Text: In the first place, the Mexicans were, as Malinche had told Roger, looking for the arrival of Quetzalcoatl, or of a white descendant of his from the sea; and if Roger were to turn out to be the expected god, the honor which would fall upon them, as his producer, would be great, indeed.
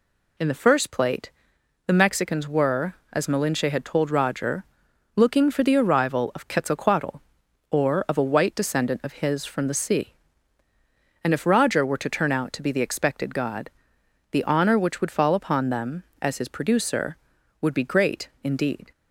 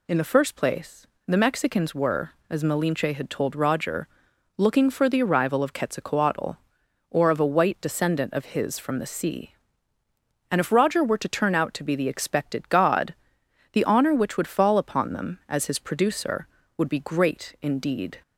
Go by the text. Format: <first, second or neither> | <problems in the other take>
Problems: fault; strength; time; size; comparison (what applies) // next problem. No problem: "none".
second | says "plate" for "place"; at 0.9 s